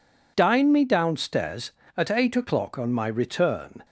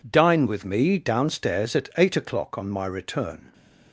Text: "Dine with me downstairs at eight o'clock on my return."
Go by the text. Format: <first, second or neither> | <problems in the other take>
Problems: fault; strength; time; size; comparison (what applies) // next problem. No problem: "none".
second | skips "with"; at 0.7 s